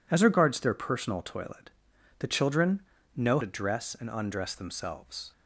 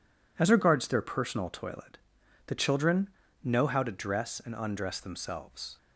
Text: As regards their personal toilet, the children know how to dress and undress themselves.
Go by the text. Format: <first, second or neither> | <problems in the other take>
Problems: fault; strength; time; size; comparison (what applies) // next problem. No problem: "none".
second | pauses between "children" and "know"; slight; at 2.8 s; 0.32 s long; slight in the second // skips "how"; at 3.4 s